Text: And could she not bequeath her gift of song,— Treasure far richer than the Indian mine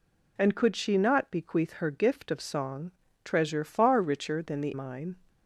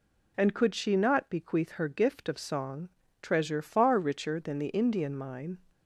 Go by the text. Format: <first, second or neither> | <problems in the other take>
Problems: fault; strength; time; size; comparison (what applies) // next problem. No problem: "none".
second | skips "Indian"; at 4.7 s